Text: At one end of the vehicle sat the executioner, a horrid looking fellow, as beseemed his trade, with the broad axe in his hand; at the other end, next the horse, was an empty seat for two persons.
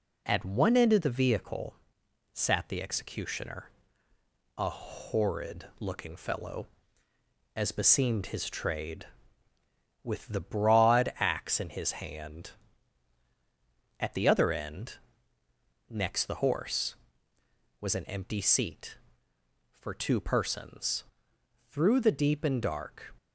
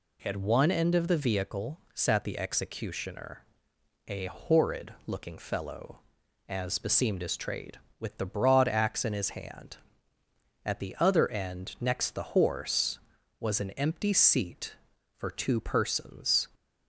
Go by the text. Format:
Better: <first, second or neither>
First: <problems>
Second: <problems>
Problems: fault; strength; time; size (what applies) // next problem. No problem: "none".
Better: second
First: pauses between "vehicle" and "sat"; noticeable; at 1.7 s; 0.58 s long // goes on to say "Through the deep and dark"; from 21.6 s on; 1.4 s long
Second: pauses between "vehicle" and "sat"; slight; at 1.7 s; 0.16 s long